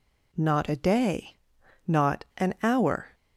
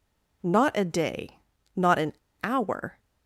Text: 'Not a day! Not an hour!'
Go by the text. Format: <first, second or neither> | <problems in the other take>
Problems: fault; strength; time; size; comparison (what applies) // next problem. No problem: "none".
first | pauses between "an" and "hour"; slight; at 2.1 s; 0.29 s long